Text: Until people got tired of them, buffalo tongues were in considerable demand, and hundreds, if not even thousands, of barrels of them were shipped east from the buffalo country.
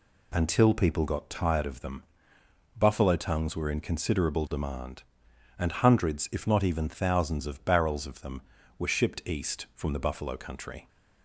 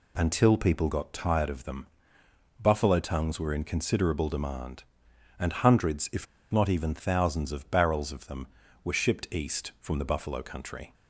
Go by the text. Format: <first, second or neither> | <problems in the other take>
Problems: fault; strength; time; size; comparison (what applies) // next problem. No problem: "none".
first | pauses between "if" and "not"; slight; at 6.2 s; 0.25 s long